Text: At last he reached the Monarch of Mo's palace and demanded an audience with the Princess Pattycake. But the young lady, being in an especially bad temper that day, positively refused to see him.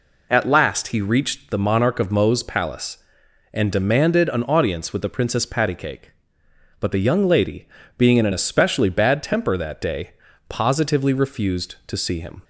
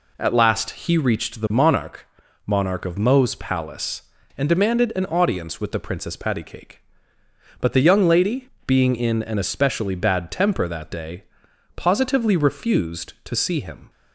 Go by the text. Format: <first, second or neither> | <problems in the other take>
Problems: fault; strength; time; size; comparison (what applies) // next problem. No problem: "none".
first | says "Monarch" twice; at 2.4 s